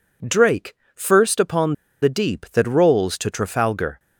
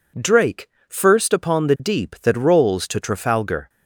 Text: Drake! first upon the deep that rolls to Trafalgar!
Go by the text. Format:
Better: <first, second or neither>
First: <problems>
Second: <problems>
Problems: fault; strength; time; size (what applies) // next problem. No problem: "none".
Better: second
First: pauses between "upon" and "the"; slight; at 1.7 s; 0.29 s long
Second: none